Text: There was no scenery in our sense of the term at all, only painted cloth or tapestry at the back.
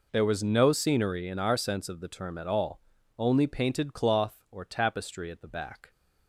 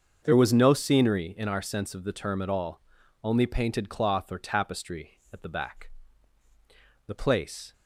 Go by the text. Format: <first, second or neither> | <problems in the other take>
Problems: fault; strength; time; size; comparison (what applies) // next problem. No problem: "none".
first | starts louder than the rest; until 1.2 s; 6.5 dB // goes on to say "The place"; noticeable; from 7.0 s on; 0.66 s long